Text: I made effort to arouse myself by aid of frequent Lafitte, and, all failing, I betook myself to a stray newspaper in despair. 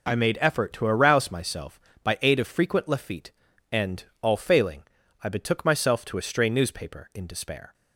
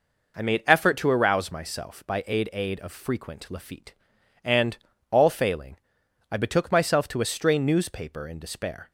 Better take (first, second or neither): first